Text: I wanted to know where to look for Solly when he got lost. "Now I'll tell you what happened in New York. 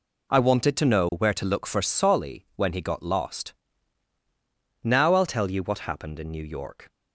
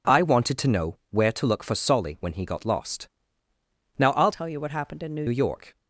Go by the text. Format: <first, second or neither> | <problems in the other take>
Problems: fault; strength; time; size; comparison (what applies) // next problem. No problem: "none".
first | changes voice from "tell" to "New"; from 4.3 to 5.2 s; 0.9 s long